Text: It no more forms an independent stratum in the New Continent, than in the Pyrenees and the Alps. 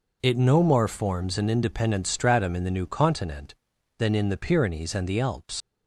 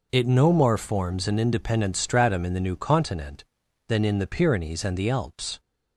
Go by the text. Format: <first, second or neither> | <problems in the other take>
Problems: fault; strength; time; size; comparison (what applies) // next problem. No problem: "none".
second | leaves "Alps" unfinished; at 5.6 s; 95 ms